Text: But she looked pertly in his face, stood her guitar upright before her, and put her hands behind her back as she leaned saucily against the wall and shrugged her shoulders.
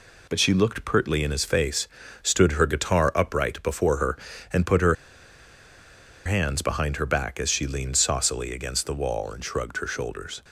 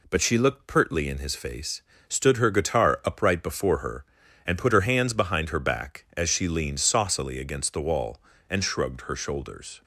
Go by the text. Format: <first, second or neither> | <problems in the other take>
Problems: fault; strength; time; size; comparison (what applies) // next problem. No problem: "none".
second | pauses between "her" and "hands"; strong; at 4.9 s; 1.3 s long